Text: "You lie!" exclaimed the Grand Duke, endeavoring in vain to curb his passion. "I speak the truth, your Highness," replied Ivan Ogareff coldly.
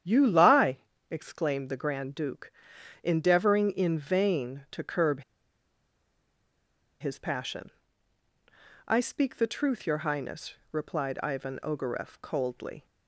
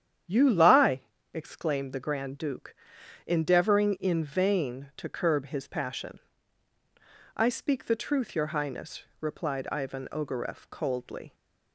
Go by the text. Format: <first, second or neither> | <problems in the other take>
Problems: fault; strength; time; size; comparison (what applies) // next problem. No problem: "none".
second | starts louder than the rest; strong; until 1.3 s; 9 dB; strong in the second // pauses between "curb" and "his"; strong; at 5.2 s; 1.7 s long